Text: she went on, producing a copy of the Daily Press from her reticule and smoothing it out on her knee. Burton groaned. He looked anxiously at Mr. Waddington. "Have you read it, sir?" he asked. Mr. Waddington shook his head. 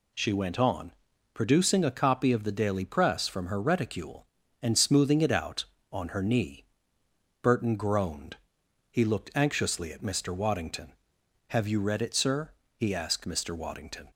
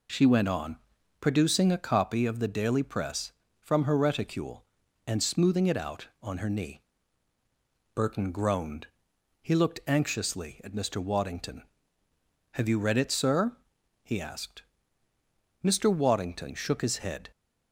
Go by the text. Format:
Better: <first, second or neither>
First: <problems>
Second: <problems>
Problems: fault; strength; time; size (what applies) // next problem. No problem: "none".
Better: second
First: stops before "shook his head"; at 14.1 s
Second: none